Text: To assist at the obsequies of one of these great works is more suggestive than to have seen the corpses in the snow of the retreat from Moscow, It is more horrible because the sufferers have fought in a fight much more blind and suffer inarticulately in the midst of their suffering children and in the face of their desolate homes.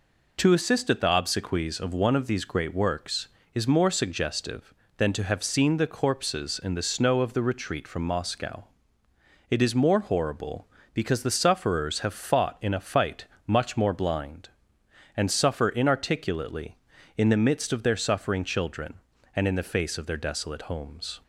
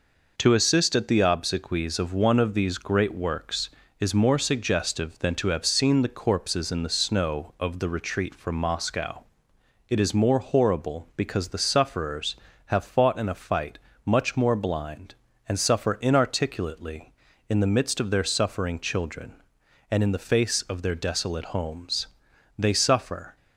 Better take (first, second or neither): first